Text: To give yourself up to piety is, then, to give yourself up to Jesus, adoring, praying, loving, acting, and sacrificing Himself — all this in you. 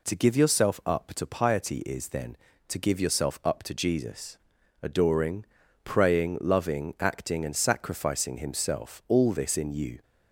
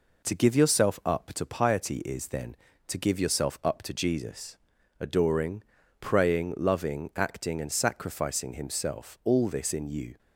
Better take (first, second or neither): first